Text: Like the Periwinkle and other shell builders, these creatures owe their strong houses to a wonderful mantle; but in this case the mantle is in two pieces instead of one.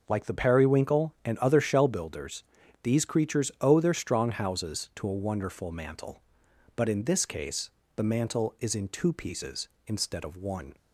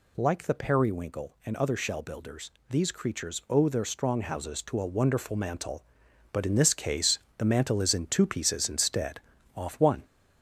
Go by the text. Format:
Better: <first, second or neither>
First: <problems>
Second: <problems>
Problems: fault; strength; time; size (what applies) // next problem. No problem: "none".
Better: first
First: pauses between "case" and "the"; slight; at 7.7 s; 0.24 s long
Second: pauses between "case" and "the"; slight; at 7.1 s; 0.20 s long // says "off" for "of"; at 9.5 s